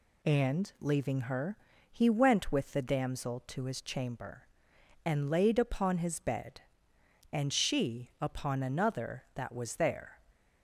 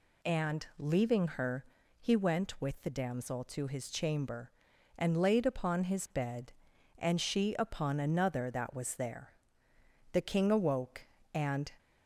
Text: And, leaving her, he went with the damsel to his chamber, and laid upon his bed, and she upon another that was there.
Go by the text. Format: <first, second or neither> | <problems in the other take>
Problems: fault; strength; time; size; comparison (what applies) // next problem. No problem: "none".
first | goes on to say "The king awoke and"; from 10.1 s on; 1.5 s long